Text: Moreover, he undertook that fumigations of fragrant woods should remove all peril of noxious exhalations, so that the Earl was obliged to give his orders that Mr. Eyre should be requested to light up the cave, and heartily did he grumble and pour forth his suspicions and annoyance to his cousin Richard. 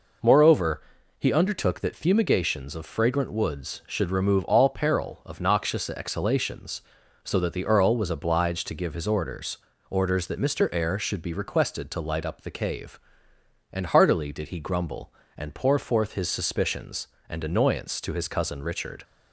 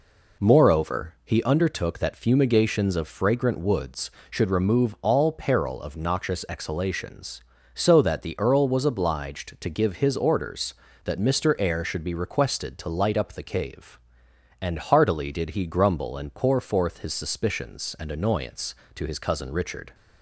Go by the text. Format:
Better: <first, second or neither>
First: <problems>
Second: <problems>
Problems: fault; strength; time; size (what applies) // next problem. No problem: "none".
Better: second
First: says "orders" twice; at 9.8 s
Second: none